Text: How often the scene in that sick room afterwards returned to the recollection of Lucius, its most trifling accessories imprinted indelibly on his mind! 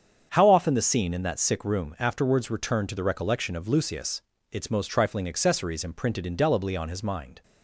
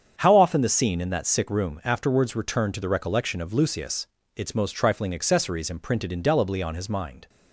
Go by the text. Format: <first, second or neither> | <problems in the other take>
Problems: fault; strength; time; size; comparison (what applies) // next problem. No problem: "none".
neither | starts louder than the rest; strong; the same in both